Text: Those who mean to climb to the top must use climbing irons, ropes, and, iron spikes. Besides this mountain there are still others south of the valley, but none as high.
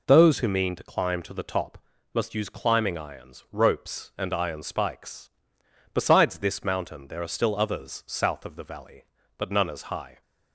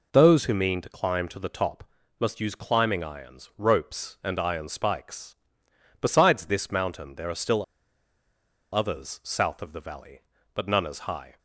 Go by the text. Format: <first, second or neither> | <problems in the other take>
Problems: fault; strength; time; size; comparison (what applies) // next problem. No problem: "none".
first | pauses between "top" and "must"; slight; at 1.8 s; 0.34 s long; slight in the first // pauses between "still" and "others"; at 7.6 s; 1.1 s long